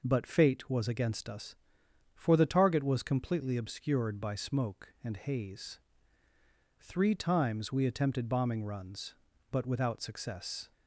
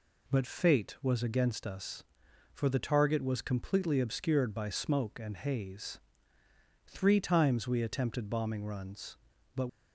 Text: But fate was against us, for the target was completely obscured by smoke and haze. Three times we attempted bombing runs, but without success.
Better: first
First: none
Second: stops before "without success"; at 9.6 s

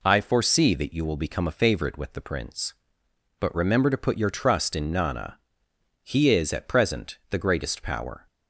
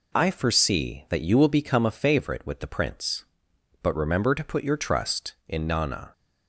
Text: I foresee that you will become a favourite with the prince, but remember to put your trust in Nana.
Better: second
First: goes on to say "He is at present the greatest power"; strong; from 6.0 s on; 2.2 s long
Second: none

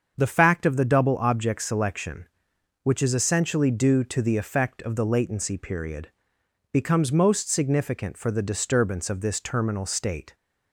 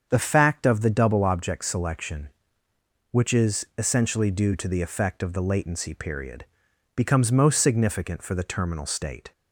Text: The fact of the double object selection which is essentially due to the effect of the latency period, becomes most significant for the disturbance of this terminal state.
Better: first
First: starts louder than the rest; until 1.2 s; 7 dB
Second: starts louder than the rest; strong; until 1.1 s; 7 dB // skips "disturbance of this"; at 8.4 s

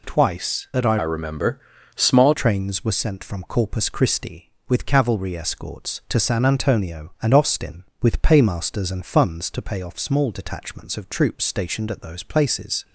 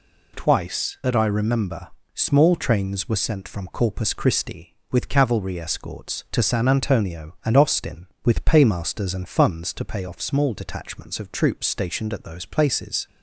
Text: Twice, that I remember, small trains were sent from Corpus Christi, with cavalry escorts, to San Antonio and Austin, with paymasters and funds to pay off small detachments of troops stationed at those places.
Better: second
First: changes voice from "remember" to "small"; from 1.0 to 2.3 s; 1.3 s long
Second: none

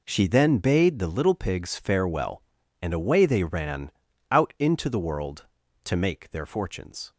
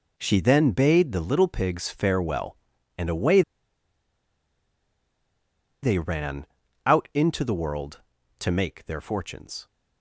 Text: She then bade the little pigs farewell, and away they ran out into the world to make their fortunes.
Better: first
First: pauses between "ran" and "out"; at 3.9 s; 0.40 s long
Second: pauses between "away" and "they"; strong; at 3.4 s; 2.4 s long // pauses between "ran" and "out"; at 6.4 s; 0.40 s long

